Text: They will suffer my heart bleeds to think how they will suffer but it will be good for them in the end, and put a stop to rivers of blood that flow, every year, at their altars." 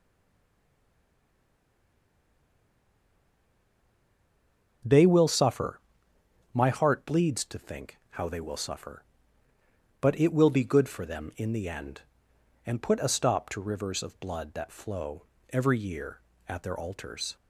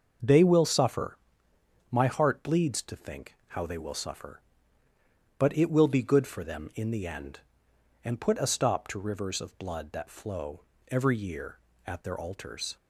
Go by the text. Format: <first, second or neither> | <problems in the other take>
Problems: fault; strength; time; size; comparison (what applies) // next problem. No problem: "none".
second | stays silent before the first word; strong; until 4.8 s; 4.8 s long // starts louder than the rest; noticeable; until 6.5 s; 6 dB; noticeable in the second // pauses between "suffer" and "my"; noticeable; at 5.7 s; 0.74 s long; noticeable in the second